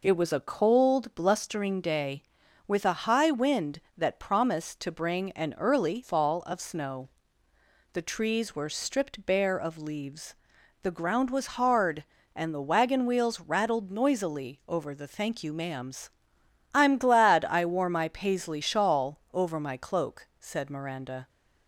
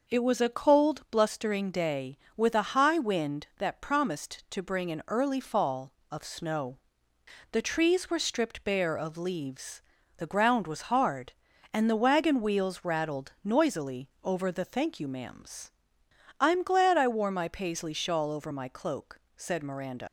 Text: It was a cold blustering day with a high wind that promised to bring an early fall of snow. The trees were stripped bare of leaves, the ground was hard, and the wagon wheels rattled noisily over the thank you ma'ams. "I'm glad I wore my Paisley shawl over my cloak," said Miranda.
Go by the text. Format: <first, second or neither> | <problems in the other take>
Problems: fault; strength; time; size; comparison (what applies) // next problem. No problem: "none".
first | leaves "Miranda" unfinished; at 20.0 s; 130 ms